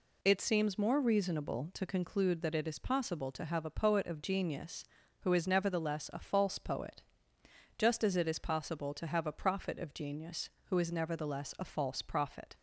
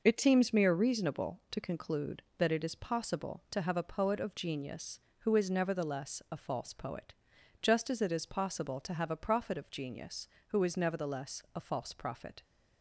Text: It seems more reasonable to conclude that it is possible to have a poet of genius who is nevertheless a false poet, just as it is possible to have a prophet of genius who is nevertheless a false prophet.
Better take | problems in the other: first | says "mere" for "more"; at 0.5 s

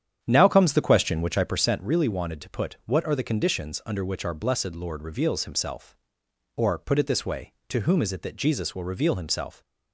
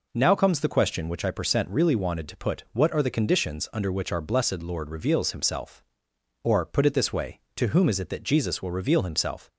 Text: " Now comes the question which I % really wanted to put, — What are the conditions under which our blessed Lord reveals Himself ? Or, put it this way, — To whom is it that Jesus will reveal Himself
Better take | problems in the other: second | starts louder than the rest; strong; until 1.8 s; 9 dB

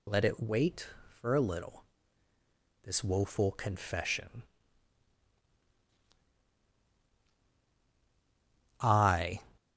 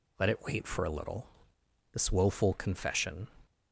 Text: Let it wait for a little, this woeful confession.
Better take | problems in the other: second | goes on to say "I"; from 8.8 s on; 0.60 s long

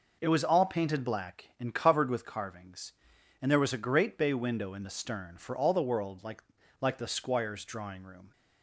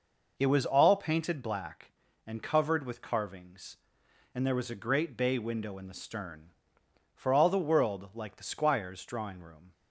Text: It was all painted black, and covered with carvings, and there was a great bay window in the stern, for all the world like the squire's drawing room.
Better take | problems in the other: second | says "like" twice; at 6.8 s

